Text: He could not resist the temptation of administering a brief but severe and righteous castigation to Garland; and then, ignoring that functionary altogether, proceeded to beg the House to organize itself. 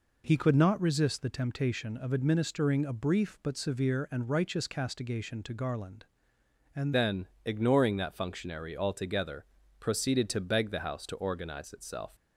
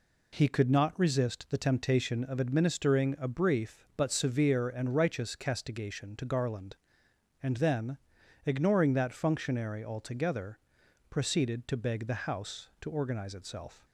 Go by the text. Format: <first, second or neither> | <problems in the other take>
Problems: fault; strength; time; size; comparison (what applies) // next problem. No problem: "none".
second | changes voice at "then"; from 6.9 s on; 5.2 s long